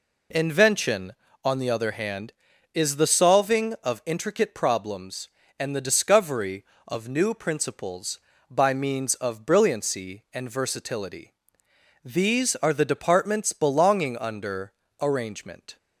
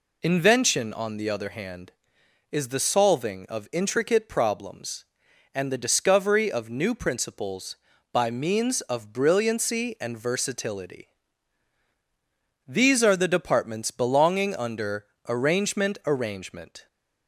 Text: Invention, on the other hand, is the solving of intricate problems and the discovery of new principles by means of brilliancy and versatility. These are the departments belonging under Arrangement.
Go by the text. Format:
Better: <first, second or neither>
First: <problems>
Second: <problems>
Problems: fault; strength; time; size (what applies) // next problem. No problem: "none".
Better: first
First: pauses between "under" and "Arrangement"; slight; at 14.7 s; 0.30 s long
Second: pauses between "under" and "Arrangement"; slight; at 15.0 s; 0.24 s long // says "Arrangement" twice; at 16.0 s